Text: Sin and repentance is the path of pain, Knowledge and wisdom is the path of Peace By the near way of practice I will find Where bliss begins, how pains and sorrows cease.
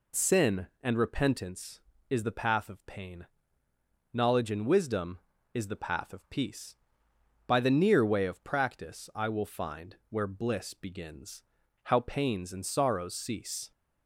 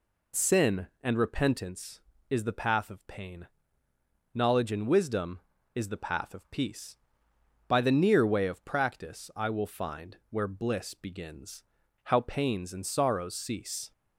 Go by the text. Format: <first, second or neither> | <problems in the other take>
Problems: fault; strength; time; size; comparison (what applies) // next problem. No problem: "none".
neither | pauses between "find" and "Where"; slight; the same in both